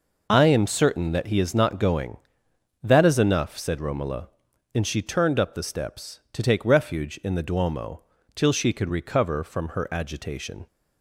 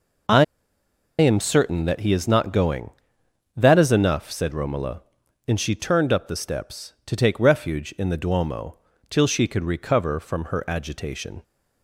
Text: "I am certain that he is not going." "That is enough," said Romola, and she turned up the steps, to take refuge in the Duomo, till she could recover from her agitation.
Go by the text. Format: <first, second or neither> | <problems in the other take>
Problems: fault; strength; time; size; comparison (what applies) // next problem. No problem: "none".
first | pauses between "I" and "am"; noticeable; at 0.4 s; 0.74 s long